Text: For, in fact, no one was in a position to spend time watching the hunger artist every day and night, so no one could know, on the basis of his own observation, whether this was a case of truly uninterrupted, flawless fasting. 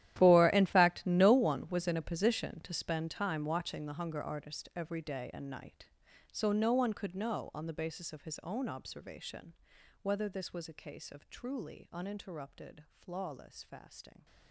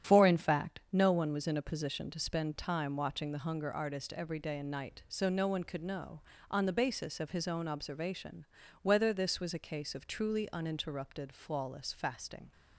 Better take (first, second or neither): second